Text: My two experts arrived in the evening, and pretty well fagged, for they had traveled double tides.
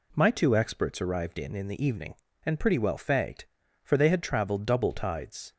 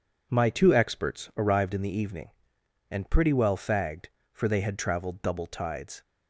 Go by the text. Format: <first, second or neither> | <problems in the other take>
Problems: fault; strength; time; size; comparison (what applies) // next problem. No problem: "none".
second | says "in" twice; at 1.5 s